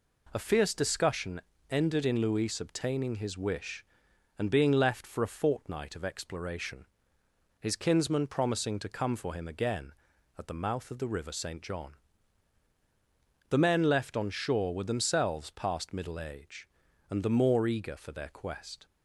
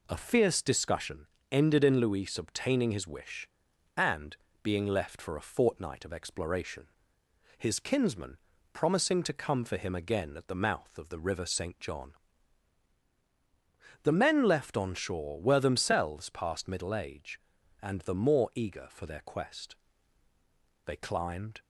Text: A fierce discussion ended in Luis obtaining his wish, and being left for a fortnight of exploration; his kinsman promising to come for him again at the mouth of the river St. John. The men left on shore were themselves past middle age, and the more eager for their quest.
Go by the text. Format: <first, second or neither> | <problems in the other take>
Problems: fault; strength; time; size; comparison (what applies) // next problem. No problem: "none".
first | pauses between "discussion" and "ended"; slight; at 1.2 s; 0.24 s long; slight in the first // pauses between "and" and "being"; slight; at 4.3 s; 0.26 s long // pauses between "kinsman" and "promising"; at 8.3 s; 0.38 s long // goes on to say "They climbed"; noticeable; from 20.8 s on; 0.78 s long